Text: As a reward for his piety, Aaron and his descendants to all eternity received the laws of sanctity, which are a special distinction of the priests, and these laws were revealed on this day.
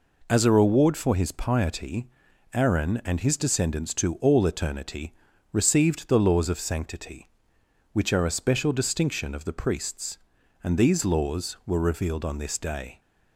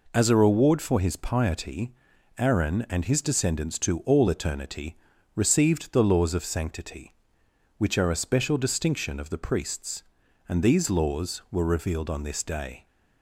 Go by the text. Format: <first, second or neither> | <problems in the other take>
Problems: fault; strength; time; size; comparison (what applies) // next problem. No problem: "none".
neither | pauses between "eternity" and "received"; the same in both